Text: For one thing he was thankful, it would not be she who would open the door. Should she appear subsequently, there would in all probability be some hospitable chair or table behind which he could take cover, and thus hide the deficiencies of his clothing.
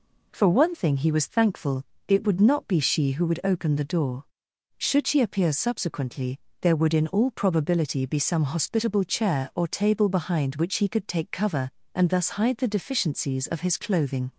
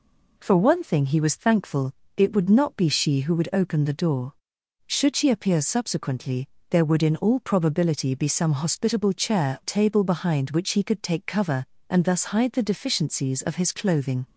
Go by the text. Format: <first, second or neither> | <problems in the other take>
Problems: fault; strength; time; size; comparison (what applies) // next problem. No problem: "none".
first | skips "or"; at 9.6 s